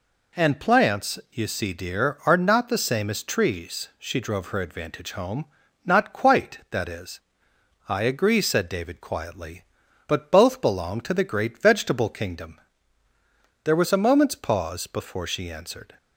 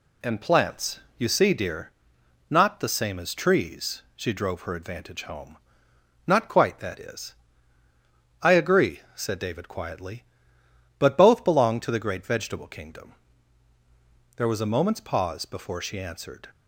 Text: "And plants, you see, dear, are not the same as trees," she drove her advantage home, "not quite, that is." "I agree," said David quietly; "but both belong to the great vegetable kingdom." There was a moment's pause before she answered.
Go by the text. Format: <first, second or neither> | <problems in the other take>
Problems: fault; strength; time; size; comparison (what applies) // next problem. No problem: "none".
first | skips "are"; at 2.1 s